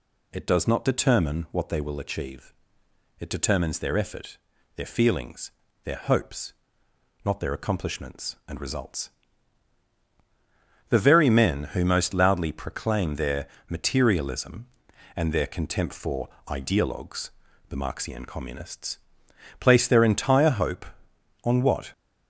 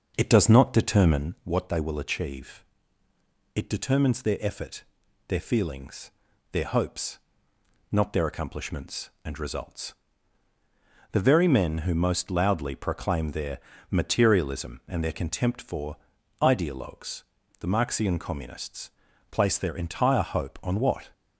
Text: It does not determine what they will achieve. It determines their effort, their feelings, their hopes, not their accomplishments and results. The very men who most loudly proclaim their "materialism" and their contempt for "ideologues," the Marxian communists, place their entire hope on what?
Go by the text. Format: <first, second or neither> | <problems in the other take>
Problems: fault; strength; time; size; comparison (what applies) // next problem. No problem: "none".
first | starts louder than the rest; until 1.3 s; 6.5 dB // pauses between "their" and "materialism"; slight; at 13.5 s; 0.32 s long; slight in the first // pauses between "for" and "ideologues"; at 15.9 s; 0.44 s long; slight in the first